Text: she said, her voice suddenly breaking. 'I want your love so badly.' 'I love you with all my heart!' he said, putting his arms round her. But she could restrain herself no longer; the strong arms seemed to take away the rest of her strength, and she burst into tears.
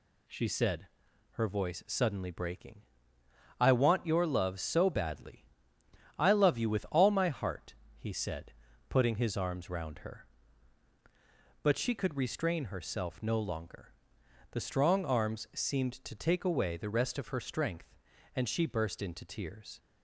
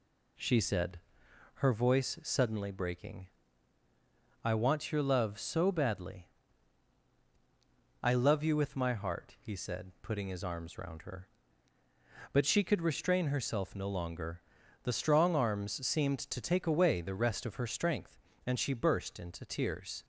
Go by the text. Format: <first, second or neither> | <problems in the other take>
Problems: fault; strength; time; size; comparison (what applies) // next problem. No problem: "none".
first | skips "all"; at 8.7 s